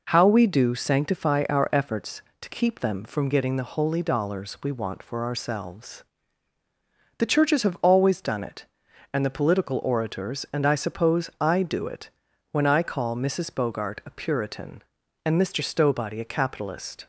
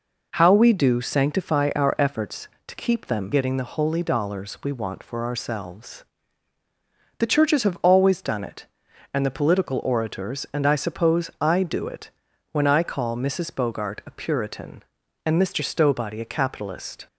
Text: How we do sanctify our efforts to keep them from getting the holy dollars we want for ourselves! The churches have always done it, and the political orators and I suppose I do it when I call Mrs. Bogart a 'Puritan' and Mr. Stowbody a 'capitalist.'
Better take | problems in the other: first | skips "from"; at 3.3 s // pauses between "it" and "when"; at 12.1 s; 0.40 s long; also in the first

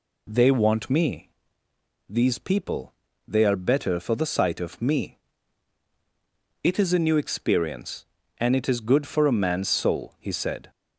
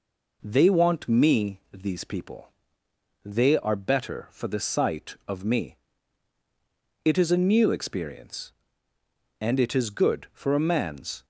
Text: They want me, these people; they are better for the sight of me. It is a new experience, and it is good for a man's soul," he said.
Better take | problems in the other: first | stops before "soul he said"; at 11.2 s

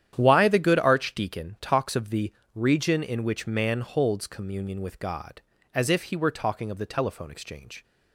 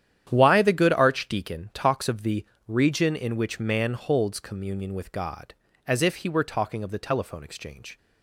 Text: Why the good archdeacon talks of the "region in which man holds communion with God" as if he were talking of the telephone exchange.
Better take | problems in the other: neither | starts louder than the rest; strong; the same in both // pauses between "the" and "region"; slight; the same in both

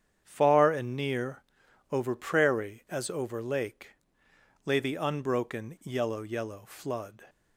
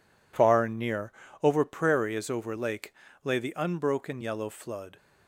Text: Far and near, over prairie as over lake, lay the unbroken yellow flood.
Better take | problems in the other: second | starts louder than the rest; strong; until 1.2 s; 8.5 dB // says "yellow" twice; at 6.2 s

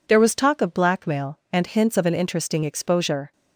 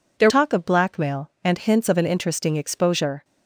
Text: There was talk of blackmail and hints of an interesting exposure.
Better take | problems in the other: first | skips "was"; at 0.2 s

